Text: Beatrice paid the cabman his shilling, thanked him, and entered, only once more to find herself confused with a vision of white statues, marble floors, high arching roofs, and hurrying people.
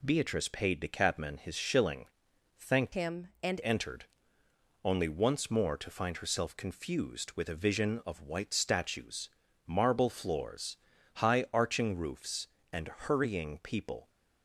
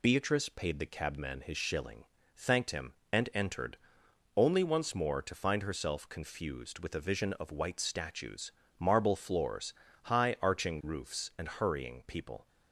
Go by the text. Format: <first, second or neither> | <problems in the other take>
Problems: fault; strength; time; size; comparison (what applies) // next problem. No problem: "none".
second | changes voice from "him" to "and"; from 2.9 to 3.6 s; 0.7 s long // pauses between "and" and "hurrying"; slight; at 12.8 s; 0.16 s long